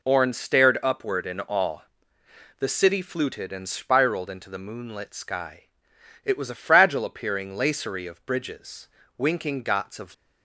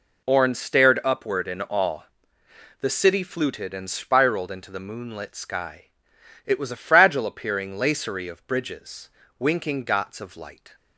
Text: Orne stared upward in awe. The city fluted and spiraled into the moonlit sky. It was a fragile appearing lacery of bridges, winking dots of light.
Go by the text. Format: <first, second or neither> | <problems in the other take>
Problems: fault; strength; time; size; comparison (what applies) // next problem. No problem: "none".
second | stops before "light"; at 10.1 s